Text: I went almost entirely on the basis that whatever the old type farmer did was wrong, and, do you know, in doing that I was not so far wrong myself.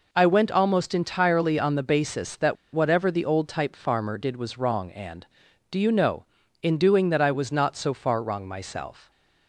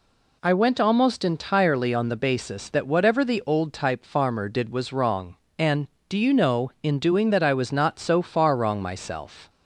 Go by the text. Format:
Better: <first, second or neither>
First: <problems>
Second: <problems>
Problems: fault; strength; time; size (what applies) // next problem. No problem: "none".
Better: second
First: pauses between "that" and "whatever"; slight; at 2.5 s; 0.18 s long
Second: none